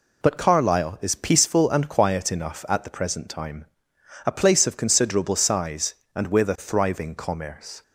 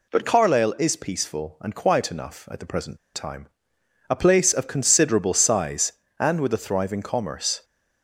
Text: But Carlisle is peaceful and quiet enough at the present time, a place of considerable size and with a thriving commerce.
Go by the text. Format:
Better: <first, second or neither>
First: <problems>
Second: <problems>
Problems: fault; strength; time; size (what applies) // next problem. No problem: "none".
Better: first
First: none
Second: pauses between "present" and "time"; slight; at 2.9 s; 0.16 s long